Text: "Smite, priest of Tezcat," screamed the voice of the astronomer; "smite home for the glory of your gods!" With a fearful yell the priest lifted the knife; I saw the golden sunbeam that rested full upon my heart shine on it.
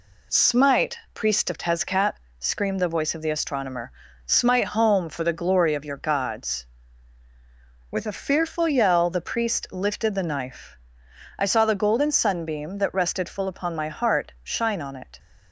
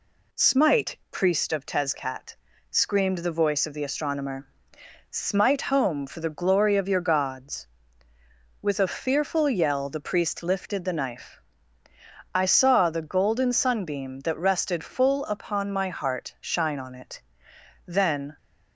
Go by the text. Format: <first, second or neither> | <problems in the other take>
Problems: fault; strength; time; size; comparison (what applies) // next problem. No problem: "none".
first | goes on to say "Then"; from 17.8 s on; 0.52 s long